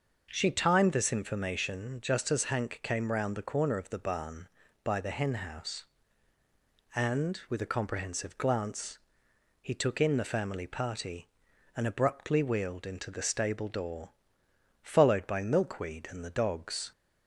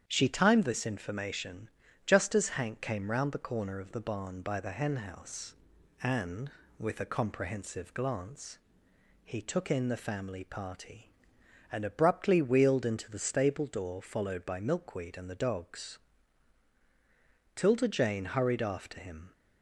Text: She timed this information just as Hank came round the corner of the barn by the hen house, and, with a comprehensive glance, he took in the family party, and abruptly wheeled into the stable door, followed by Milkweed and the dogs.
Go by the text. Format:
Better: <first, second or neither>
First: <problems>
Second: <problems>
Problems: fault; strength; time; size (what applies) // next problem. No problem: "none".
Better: first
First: none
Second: starts louder than the rest; strong; until 1.0 s; 8.5 dB // pauses between "information" and "just"; slight; at 1.6 s; 0.36 s long // goes on to say "Tilda Jane hurried after him"; strong; from 17.5 s on; 1.7 s long